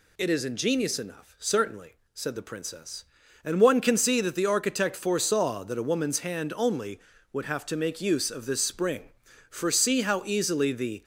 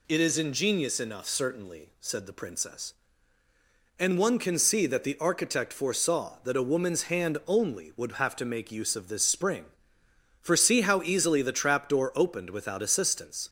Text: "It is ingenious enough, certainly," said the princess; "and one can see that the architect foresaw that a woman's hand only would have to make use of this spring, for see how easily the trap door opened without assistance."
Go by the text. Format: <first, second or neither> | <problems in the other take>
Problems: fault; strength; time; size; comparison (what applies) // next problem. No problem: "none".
second | stops before "trap door opened without assistance"; at 11.0 s